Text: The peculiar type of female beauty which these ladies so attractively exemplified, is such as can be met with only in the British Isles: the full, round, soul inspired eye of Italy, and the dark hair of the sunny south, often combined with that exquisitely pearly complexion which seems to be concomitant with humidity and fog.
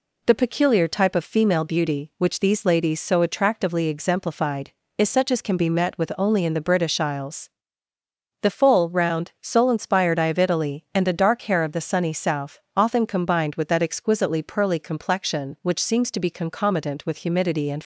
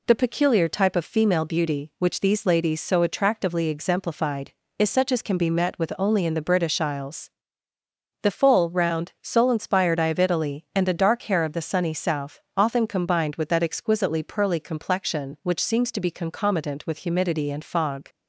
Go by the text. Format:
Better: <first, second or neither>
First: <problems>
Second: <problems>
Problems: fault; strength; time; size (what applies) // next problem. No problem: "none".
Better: second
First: stops before "fog"; at 17.8 s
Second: none